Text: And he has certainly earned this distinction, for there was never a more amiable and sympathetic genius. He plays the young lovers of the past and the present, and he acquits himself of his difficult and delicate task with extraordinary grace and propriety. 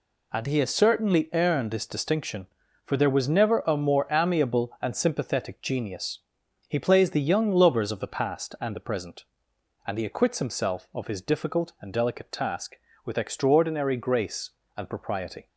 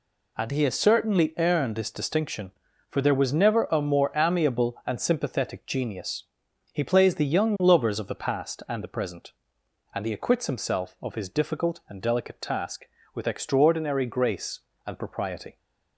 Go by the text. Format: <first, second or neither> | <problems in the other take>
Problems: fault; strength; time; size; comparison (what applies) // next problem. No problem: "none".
neither | none